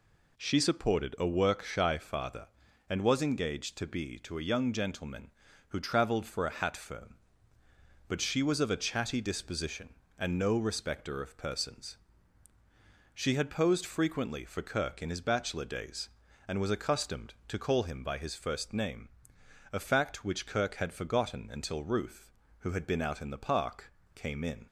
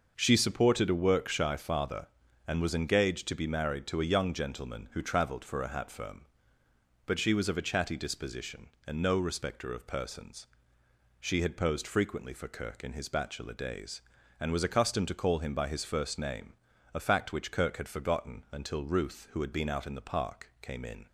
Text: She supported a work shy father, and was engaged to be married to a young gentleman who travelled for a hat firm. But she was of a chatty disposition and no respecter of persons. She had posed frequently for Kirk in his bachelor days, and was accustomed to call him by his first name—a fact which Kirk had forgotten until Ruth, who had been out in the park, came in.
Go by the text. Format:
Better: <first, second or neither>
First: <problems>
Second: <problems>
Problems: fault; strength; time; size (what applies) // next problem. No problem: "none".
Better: second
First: skips "married"; at 4.1 s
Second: none